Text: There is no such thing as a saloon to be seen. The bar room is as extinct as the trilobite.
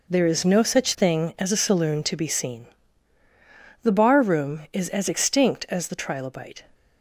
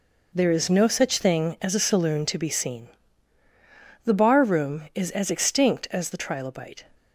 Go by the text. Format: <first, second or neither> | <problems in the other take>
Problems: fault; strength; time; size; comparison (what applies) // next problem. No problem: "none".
neither | none